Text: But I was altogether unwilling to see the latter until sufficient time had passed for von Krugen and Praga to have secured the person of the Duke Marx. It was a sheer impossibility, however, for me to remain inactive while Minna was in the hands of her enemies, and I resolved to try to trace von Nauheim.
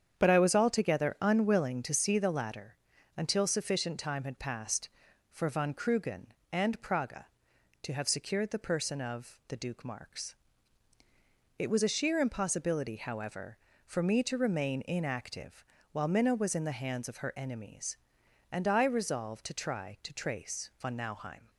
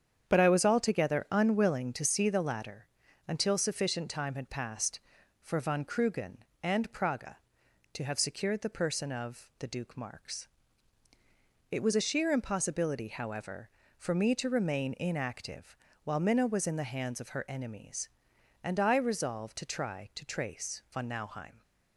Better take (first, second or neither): neither